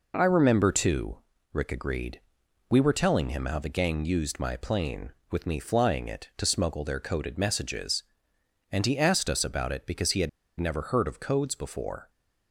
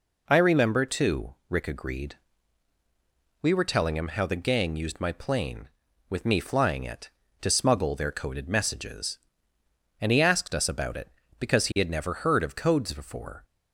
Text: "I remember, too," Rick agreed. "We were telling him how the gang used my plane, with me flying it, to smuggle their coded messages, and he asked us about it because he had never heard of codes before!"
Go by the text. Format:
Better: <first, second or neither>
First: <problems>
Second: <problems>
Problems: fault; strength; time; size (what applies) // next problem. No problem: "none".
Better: second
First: pauses between "had" and "never"; slight; at 10.2 s; 0.29 s long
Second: none